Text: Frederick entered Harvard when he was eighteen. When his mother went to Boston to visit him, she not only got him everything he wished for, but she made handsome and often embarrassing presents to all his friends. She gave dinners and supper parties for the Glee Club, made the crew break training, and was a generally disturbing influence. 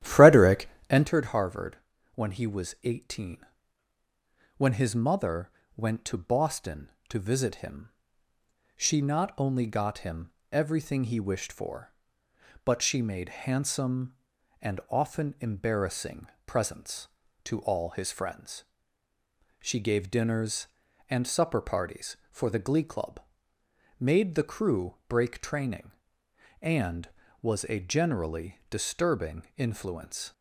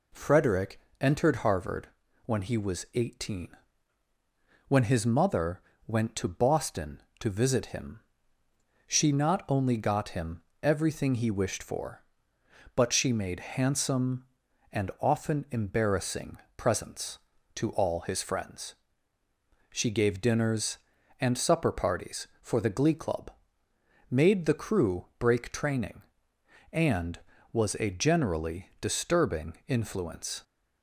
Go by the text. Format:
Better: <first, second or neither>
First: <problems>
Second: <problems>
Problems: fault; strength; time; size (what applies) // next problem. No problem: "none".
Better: second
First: starts louder than the rest; strong; until 1.1 s; 12.5 dB // pauses between "Frederick" and "entered"; slight; at 0.6 s; 0.22 s long // pauses between "Harvard" and "when"; slight; at 1.7 s; 0.36 s long // pauses between "mother" and "went"; slight; at 5.5 s; 0.24 s long // pauses between "him" and "everything"; slight; at 10.3 s; 0.20 s long // pauses between "embarrassing" and "presents"; slight; at 16.2 s; 0.18 s long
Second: pauses between "Frederick" and "entered"; slight; at 0.7 s; 0.22 s long // pauses between "Harvard" and "when"; slight; at 1.8 s; 0.36 s long // pauses between "mother" and "went"; slight; at 5.6 s; 0.24 s long // pauses between "him" and "everything"; slight; at 10.4 s; 0.20 s long // pauses between "embarrassing" and "presents"; slight; at 16.3 s; 0.18 s long